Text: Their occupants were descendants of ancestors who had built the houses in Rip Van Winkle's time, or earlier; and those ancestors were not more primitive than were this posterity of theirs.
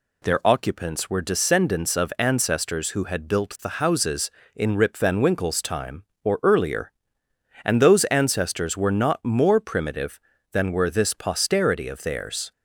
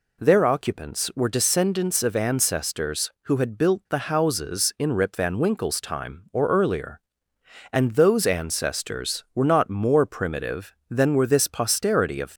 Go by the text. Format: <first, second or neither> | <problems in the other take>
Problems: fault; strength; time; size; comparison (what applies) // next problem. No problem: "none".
first | stops before "theirs"; at 12.3 s